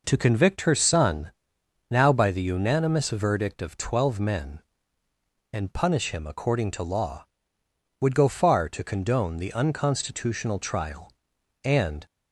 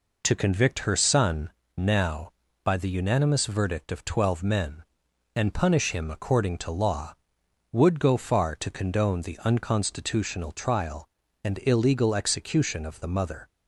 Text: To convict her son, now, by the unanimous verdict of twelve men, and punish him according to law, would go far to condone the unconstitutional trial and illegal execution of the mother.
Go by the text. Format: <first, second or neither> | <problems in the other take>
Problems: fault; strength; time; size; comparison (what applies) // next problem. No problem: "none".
second | stops before "illegal execution of the mother"; at 12.0 s